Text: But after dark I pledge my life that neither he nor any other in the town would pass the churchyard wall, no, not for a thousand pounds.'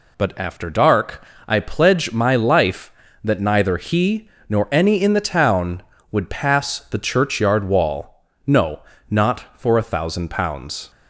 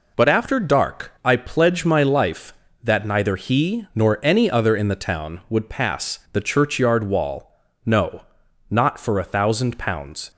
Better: second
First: pauses between "dark" and "I"; slight; at 1.2 s; 0.26 s long // pauses between "he" and "nor"; slight; at 4.2 s; 0.20 s long // skips "other"; at 5.0 s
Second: none

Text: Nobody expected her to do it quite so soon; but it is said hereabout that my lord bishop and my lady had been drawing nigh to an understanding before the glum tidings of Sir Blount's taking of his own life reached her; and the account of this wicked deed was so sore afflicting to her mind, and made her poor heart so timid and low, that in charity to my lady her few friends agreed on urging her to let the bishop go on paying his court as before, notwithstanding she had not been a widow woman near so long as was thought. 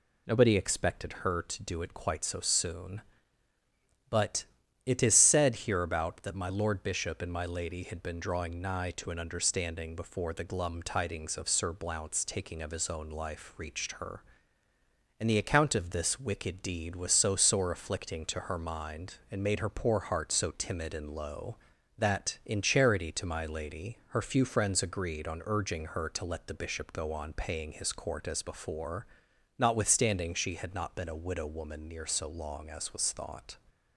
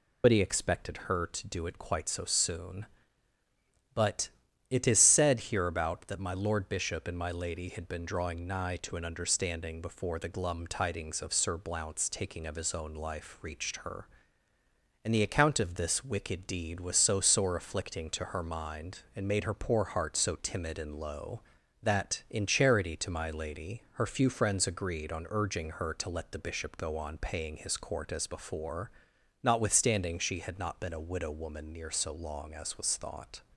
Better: first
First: pauses between "but" and "it"; at 4.4 s; 0.40 s long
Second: loses the start of "Nobody"; at 0.2 s; 125 ms // pauses between "but" and "it"; at 4.2 s; 0.40 s long

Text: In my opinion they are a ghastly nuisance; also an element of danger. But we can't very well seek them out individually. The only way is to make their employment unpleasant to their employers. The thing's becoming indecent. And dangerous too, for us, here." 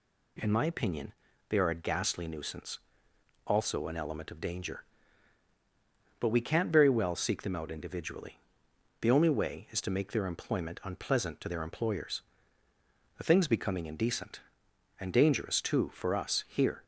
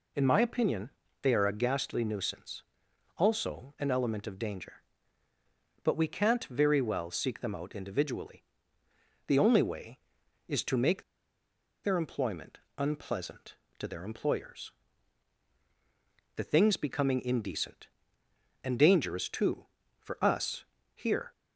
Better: first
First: pauses between "opinion" and "they"; slight; at 1.1 s; 0.36 s long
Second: pauses between "opinion" and "they"; slight; at 0.9 s; 0.32 s long // pauses between "make" and "their"; noticeable; at 11.0 s; 0.81 s long // pauses between "employment" and "unpleasant"; slight; at 12.5 s; 0.18 s long

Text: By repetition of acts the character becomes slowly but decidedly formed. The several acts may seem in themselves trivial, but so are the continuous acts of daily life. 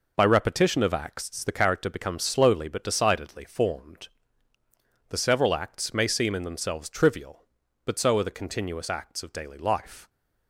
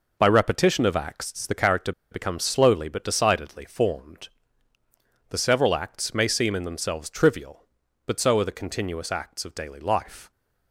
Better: first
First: none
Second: pauses between "character" and "becomes"; slight; at 1.9 s; 0.19 s long

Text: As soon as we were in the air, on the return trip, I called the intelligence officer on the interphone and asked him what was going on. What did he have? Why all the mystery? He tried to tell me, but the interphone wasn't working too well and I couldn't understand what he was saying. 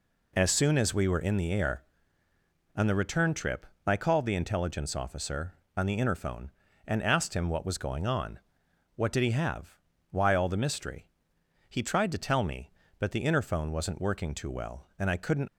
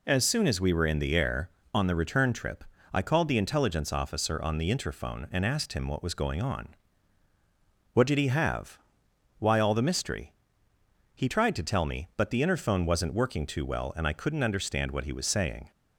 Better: second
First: stops before "understand what he was saying"; at 15.4 s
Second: none

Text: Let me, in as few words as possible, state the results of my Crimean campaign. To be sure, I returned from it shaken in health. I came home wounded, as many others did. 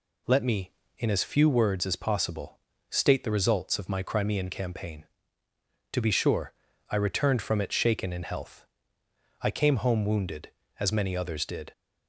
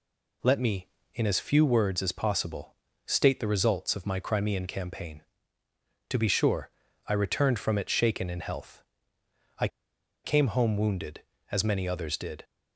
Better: first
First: none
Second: pauses between "I" and "came"; noticeable; at 9.6 s; 0.56 s long

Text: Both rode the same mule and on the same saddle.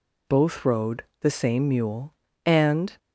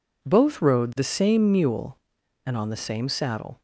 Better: second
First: pauses between "rode" and "the"; slight; at 1.0 s; 0.16 s long // stops before "on the same saddle"; at 2.9 s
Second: none

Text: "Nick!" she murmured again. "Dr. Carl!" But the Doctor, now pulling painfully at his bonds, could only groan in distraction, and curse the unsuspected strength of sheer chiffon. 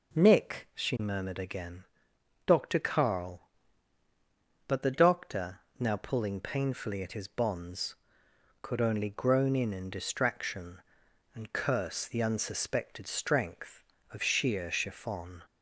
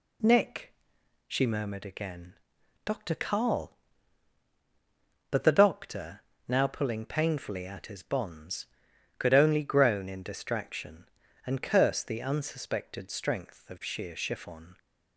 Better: second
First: says "in" twice; at 9.7 s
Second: none

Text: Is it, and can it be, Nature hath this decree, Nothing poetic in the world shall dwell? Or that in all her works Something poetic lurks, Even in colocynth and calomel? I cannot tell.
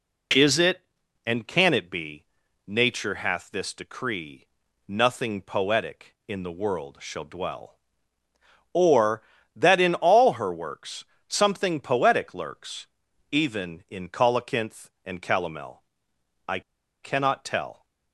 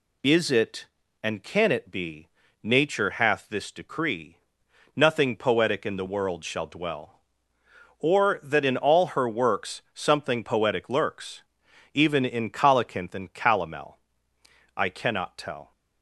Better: second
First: pauses between "works" and "Something"; slight; at 11.0 s; 0.24 s long // pauses between "I" and "cannot"; at 16.5 s; 0.43 s long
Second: none

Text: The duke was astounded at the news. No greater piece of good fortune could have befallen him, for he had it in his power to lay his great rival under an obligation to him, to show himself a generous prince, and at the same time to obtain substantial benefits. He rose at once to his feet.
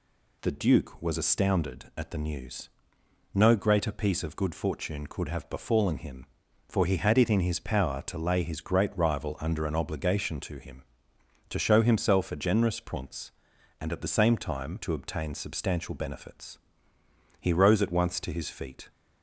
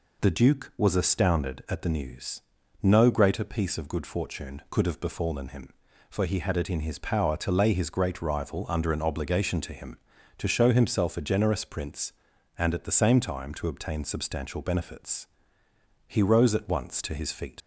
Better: first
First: none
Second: leaves "feet" unfinished; at 17.6 s; 80 ms

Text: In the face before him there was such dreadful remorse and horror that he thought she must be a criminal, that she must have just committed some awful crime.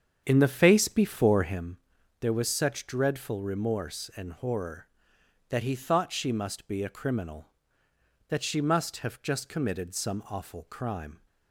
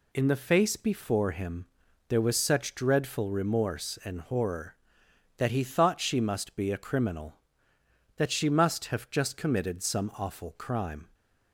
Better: second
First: starts louder than the rest; strong; until 1.7 s; 7.5 dB // pauses between "him" and "there"; at 1.7 s; 0.44 s long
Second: pauses between "him" and "there"; at 1.6 s; 0.44 s long

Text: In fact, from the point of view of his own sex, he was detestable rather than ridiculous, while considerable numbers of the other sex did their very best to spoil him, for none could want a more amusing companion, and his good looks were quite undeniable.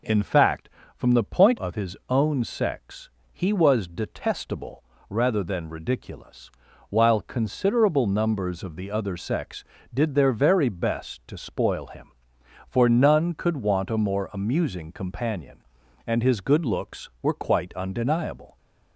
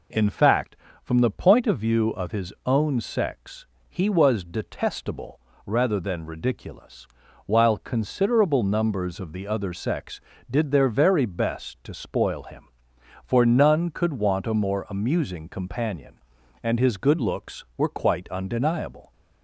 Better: second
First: skips "of view"; at 1.5 s // pauses between "detestable" and "rather"; slight; at 4.8 s; 0.26 s long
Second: pauses between "detestable" and "rather"; slight; at 5.3 s; 0.26 s long

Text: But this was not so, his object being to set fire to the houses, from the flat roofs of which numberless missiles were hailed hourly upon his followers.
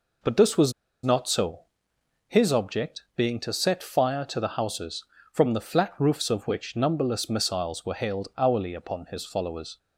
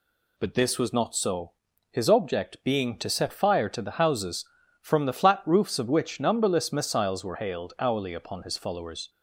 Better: second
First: pauses between "was" and "not"; slight; at 0.7 s; 0.31 s long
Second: none

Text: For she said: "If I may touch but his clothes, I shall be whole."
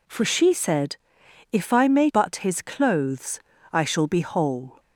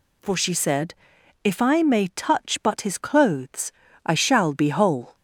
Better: second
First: skips "touch"; at 2.1 s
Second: none

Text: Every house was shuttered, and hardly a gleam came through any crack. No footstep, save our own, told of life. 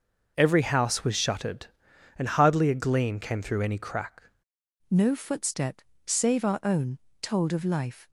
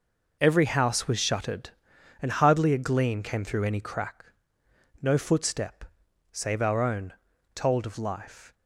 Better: second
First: changes voice at "No"; from 4.8 s on; 3.2 s long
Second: none

